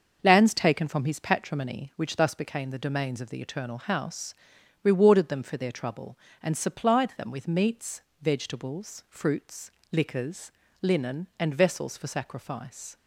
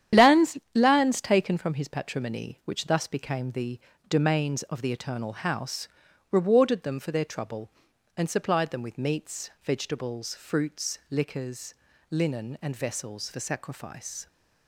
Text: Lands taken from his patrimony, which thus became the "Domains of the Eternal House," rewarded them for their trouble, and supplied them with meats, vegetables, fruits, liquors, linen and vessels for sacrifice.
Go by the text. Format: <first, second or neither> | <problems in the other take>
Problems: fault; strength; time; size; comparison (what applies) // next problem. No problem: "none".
first | starts louder than the rest; strong; until 1.3 s; 10 dB; also in the first // says "Lands" twice; at 0.7 s // pauses between "the" and "Domains"; slight; at 3.7 s; 0.28 s long